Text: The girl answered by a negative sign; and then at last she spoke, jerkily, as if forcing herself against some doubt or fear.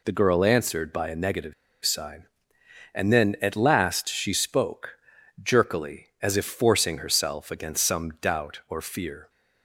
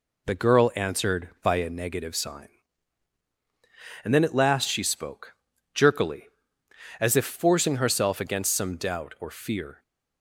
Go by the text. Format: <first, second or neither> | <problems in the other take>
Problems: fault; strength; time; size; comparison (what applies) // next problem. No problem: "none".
second | pauses between "negative" and "sign"; slight; at 1.5 s; 0.31 s long